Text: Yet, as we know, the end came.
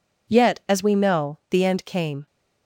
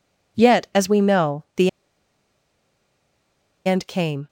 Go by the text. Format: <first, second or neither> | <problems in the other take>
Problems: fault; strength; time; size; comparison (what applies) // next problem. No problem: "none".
first | pauses between "the" and "end"; strong; at 1.6 s; 1.9 s long